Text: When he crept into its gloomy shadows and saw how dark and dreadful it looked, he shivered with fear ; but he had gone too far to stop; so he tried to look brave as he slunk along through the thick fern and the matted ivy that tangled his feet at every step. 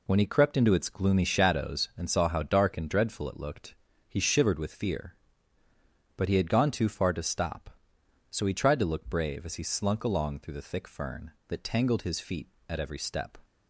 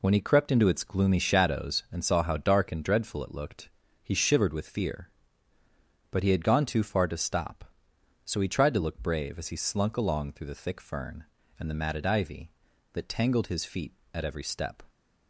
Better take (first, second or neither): second